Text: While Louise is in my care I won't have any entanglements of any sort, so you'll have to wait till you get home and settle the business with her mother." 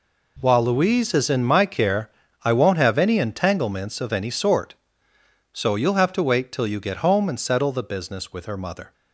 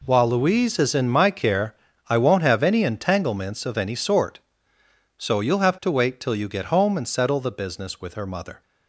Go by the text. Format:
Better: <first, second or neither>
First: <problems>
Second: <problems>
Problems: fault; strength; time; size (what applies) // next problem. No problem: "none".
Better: neither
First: pauses between "care" and "I"; slight; at 2.0 s; 0.34 s long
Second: pauses between "care" and "I"; slight; at 1.7 s; 0.34 s long